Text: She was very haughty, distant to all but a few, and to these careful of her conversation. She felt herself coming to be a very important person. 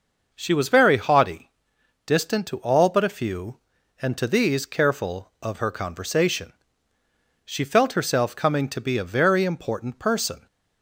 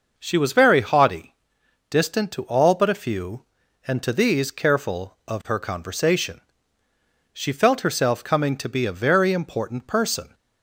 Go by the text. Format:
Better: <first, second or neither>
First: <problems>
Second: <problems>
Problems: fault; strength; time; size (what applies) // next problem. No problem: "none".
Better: neither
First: none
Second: none